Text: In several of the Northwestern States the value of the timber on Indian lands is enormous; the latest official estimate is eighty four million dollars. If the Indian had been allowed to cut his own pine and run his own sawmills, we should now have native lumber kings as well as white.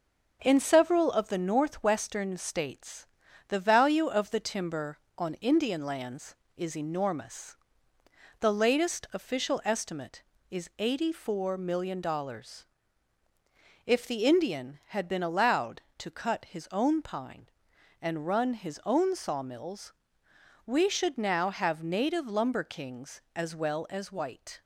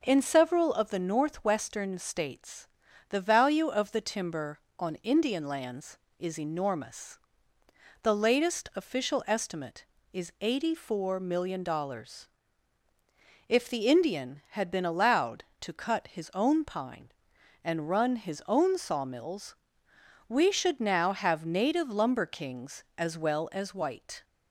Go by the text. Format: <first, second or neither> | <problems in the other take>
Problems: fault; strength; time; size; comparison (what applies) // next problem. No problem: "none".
second | gets quieter; noticeable; throughout; 4 dB // starts louder than the rest; until 1.4 s; 6.5 dB; noticeable in the second // pauses between "States" and "the"; at 3.0 s; 0.44 s long; also in the second